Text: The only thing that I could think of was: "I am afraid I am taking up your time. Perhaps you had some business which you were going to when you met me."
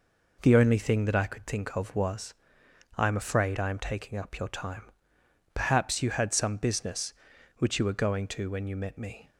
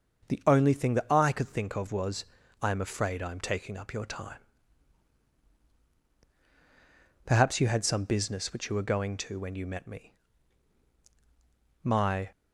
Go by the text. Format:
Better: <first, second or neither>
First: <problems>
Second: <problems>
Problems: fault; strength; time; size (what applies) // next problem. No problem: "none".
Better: first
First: none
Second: starts louder than the rest; until 1.3 s; 6 dB // goes on to say "My"; slight; from 11.8 s on; 0.46 s long